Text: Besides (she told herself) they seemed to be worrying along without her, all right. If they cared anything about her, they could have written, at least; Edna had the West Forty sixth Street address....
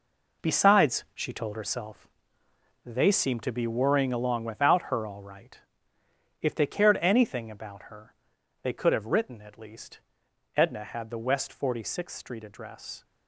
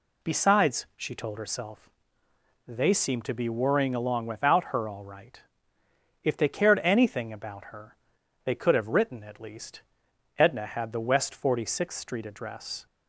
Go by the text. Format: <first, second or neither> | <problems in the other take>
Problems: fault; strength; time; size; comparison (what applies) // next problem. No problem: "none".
second | gets quieter; strong; throughout; 9.5 dB